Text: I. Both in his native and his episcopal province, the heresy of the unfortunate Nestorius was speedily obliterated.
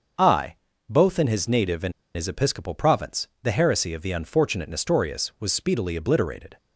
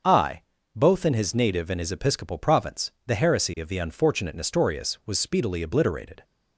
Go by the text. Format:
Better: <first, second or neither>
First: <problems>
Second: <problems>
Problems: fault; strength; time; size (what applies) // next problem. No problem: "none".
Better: second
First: starts louder than the rest; until 1.5 s; 6.5 dB // pauses between "and" and "his"; slight; at 1.9 s; 0.24 s long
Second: starts louder than the rest; until 1.3 s; 6.5 dB